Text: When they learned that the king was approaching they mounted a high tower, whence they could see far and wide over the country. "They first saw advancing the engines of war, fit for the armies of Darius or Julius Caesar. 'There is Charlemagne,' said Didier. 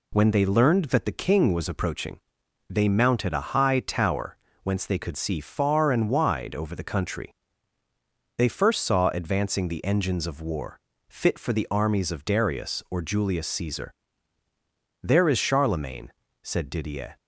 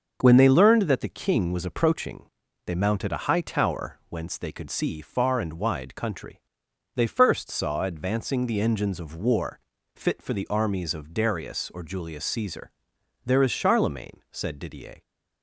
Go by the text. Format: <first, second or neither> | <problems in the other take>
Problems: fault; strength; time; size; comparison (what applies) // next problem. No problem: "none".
first | starts louder than the rest; until 1.2 s; 6.5 dB // pauses between "approaching" and "they"; at 2.2 s; 0.42 s long; noticeable in the first // skips "over the"; at 5.9 s